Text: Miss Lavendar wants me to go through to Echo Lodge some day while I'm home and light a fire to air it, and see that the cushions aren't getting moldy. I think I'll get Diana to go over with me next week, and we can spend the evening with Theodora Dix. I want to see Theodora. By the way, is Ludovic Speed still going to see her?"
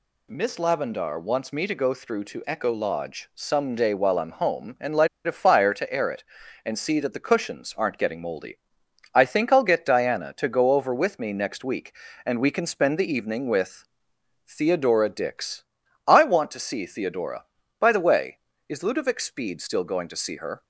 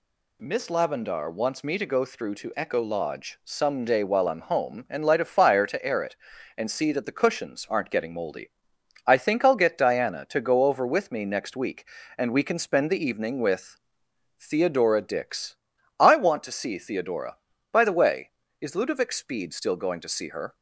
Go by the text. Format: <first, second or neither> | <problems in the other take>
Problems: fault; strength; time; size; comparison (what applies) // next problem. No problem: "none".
second | pauses between "light" and "a"; slight; at 5.0 s; 0.17 s long // pauses between "with" and "Theodora"; noticeable; at 13.8 s; 0.64 s long; noticeable in the second